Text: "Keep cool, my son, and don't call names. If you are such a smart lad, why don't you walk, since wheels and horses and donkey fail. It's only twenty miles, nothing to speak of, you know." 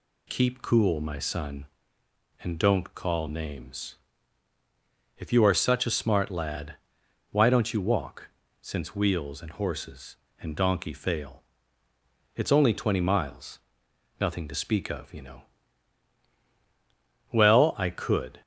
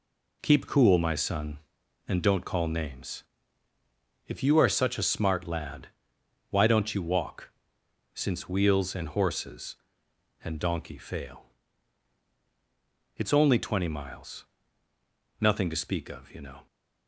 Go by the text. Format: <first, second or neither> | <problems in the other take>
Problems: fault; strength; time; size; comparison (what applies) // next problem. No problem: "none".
second | goes on to say "Well I could"; noticeable; from 17.3 s on; 1.1 s long